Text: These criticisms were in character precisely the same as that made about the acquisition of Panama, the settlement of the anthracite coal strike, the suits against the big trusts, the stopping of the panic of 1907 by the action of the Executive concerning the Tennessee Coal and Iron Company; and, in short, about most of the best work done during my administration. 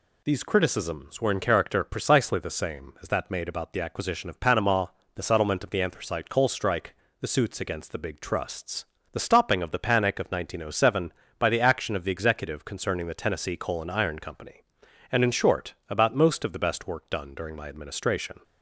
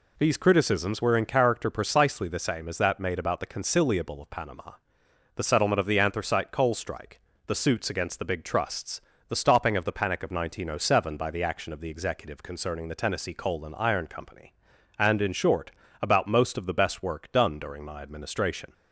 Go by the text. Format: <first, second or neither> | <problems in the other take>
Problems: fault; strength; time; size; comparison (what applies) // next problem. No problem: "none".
first | says "conciliable" for "acquisition"; at 3.4 s